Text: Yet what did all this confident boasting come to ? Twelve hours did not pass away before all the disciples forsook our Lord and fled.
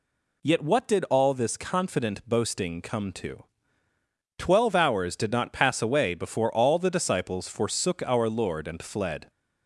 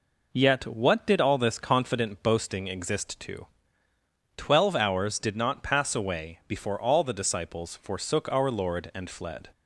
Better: first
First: none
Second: says "exist" for "come"; at 2.6 s

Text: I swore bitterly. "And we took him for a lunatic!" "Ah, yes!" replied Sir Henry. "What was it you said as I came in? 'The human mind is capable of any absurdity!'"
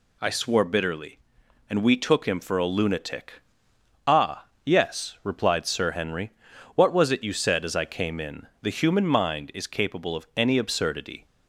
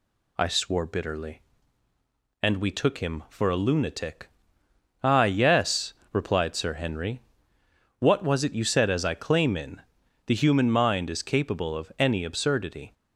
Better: first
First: none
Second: says "claim" for "came"; at 9.1 s

